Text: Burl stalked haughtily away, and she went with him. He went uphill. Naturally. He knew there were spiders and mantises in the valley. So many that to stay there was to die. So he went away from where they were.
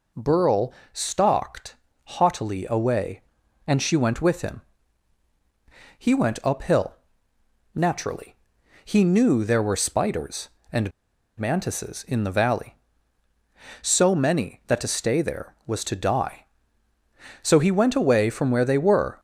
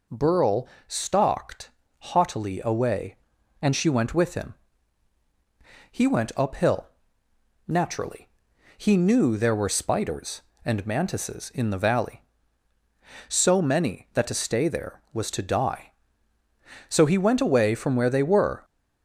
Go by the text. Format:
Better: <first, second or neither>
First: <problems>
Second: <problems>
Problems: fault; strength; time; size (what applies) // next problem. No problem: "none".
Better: second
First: pauses between "Burl" and "stalked"; slight; at 0.7 s; 0.20 s long // pauses between "stalked" and "haughtily"; slight; at 1.7 s; 0.30 s long // pauses between "and" and "mantises"; noticeable; at 10.9 s; 0.48 s long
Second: pauses between "Burl" and "stalked"; slight; at 0.6 s; 0.20 s long // pauses between "stalked" and "haughtily"; slight; at 1.6 s; 0.30 s long